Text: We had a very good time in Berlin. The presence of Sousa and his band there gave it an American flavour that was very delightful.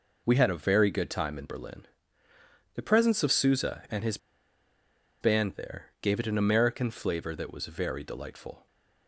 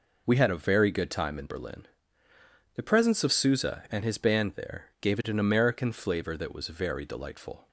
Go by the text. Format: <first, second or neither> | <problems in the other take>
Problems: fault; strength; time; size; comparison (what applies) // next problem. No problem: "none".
second | pauses between "his" and "band"; at 4.1 s; 1.0 s long // pauses between "there" and "gave"; slight; at 5.8 s; 0.16 s long; slight in the second